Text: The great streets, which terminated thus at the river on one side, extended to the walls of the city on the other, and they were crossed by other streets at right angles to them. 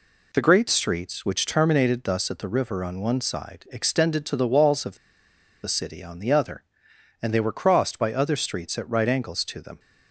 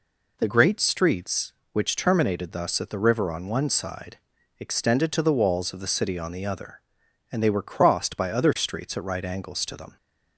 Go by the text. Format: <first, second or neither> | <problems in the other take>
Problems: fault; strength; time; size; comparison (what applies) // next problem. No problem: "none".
second | pauses between "of" and "the"; noticeable; at 4.9 s; 0.67 s long